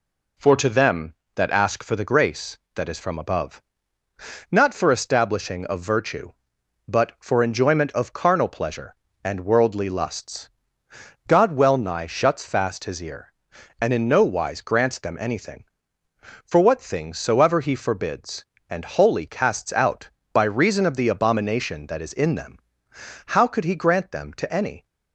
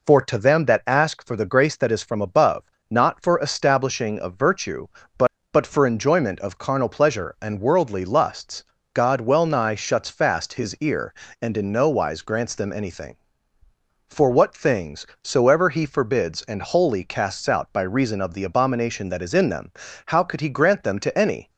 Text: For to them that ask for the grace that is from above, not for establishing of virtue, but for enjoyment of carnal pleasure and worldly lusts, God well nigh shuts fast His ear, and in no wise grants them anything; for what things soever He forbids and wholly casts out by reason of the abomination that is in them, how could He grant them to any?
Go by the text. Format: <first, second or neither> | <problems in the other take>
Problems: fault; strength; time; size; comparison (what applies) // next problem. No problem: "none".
first | says "but" twice; at 5.5 s // pauses between "things" and "soever"; slight; at 15.0 s; 0.16 s long